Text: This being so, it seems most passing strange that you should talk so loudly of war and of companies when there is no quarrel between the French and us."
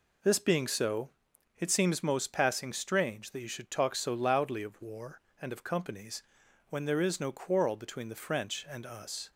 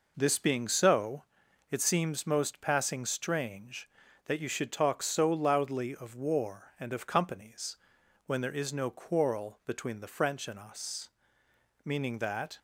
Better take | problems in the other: first | pauses between "companies" and "when"; noticeable; at 7.7 s; 0.50 s long; noticeable in the first // goes on to say "Meaning that"; noticeable; from 11.8 s on; 0.76 s long

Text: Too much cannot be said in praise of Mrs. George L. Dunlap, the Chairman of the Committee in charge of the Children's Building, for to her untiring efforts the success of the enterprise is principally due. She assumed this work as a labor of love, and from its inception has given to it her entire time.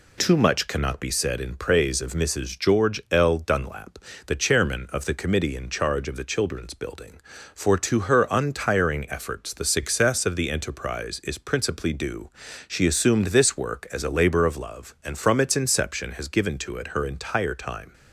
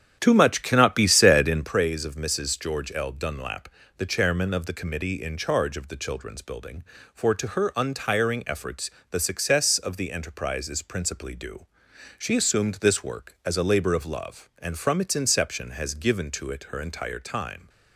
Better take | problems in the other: first | starts louder than the rest; strong; until 1.7 s; 9.5 dB // pauses between "efforts" and "the"; slight; at 8.9 s; 0.20 s long

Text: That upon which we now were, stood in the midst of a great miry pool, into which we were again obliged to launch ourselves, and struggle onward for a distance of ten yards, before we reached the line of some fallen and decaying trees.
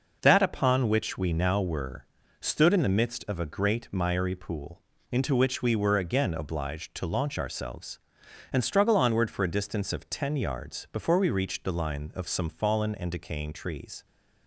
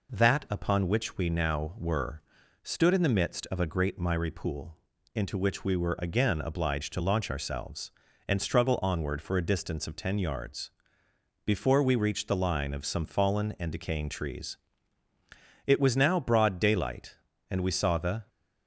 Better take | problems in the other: first | goes on to say "It was now broad daylight and we saw the"; strong; from 15.6 s on; 2.6 s long

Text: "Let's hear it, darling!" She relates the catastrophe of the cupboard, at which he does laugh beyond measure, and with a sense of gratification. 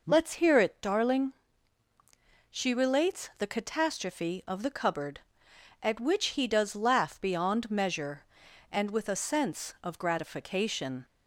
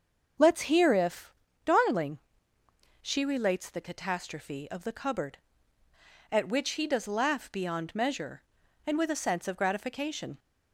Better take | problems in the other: first | starts louder than the rest; until 1.7 s; 6.5 dB // says "if" for "it"; at 0.9 s

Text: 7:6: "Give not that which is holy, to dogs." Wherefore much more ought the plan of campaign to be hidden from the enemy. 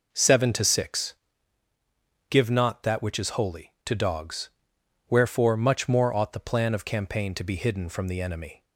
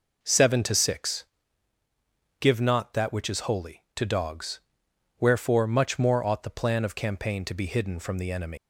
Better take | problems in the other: first | leaves "enemy" unfinished; at 8.5 s; 170 ms

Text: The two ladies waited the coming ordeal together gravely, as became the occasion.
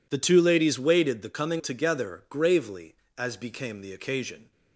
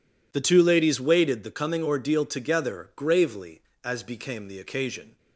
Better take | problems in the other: second | skips "ordeal"; at 1.5 s

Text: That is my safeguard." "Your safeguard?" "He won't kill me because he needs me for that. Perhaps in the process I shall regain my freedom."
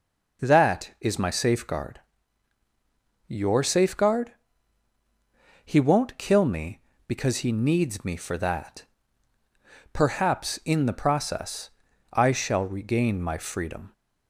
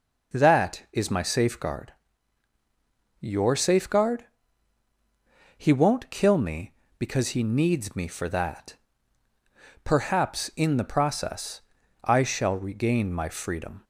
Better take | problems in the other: neither | pauses between "process" and "I"; the same in both

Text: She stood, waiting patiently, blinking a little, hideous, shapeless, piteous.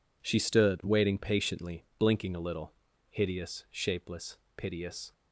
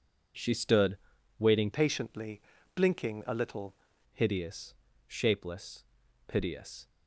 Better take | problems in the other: first | changes voice from "patiently" to "little"; from 1.7 to 3.7 s; 2.0 s long

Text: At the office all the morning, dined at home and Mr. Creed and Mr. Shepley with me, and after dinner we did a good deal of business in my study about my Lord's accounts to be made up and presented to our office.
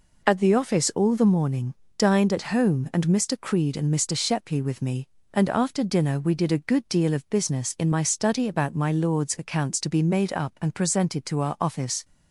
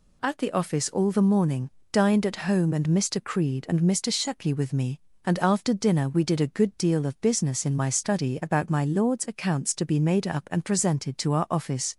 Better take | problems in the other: neither | none

